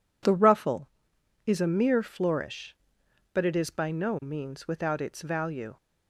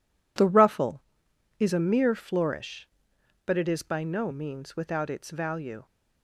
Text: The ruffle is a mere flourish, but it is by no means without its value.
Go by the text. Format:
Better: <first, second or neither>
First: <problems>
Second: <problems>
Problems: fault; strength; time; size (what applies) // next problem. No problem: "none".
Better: first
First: none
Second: gets quieter; strong; throughout; 11 dB